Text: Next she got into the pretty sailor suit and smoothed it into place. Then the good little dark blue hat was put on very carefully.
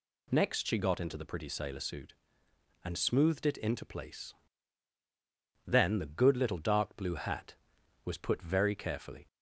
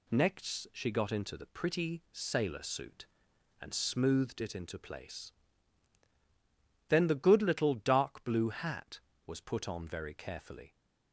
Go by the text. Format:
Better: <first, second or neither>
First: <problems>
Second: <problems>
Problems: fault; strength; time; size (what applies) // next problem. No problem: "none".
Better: second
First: skips "on"; at 8.4 s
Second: none